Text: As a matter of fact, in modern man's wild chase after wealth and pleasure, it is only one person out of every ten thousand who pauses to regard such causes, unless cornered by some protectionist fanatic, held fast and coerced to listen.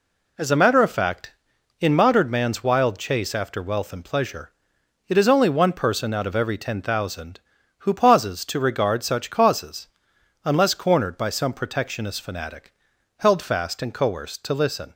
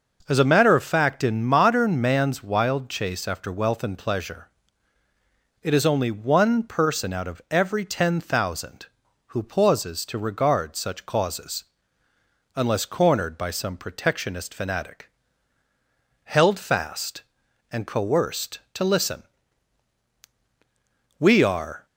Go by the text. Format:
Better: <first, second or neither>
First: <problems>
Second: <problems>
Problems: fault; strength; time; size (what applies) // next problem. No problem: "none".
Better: first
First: none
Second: goes on to say "We are"; noticeable; from 21.1 s on; 0.66 s long